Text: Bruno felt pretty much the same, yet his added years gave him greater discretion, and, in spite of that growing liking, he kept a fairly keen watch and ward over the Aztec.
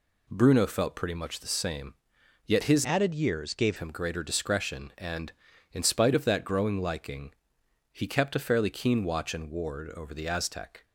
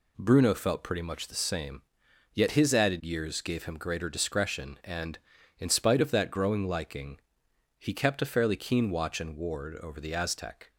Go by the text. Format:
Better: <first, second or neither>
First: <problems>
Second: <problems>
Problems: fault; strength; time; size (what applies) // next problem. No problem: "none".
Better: second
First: changes voice from "added" to "gave"; from 2.8 to 3.7 s; 0.9 s long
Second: none